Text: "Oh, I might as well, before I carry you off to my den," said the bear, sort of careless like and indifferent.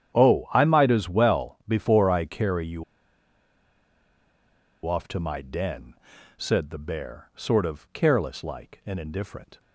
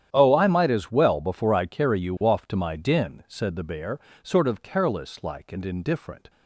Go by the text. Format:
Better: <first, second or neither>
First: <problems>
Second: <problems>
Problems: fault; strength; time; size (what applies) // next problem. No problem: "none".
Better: second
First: starts louder than the rest; strong; until 1.2 s; 10 dB // pauses between "you" and "off"; strong; at 2.8 s; 2.0 s long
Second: starts louder than the rest; strong; until 1.1 s; 10 dB